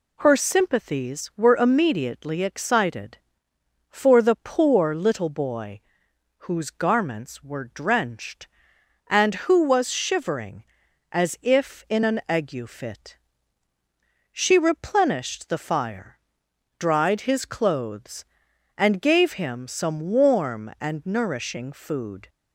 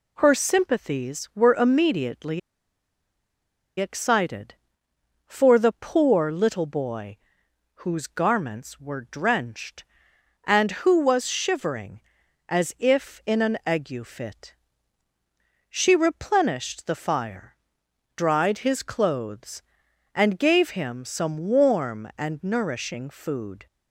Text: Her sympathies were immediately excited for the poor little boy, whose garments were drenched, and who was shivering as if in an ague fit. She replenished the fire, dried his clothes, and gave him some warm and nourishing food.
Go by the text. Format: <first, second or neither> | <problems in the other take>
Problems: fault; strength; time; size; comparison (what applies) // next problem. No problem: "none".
first | pauses between "immediately" and "excited"; strong; at 2.3 s; 1.4 s long